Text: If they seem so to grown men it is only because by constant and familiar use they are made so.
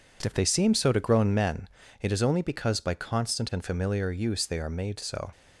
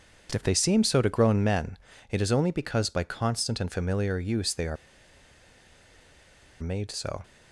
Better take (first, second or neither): first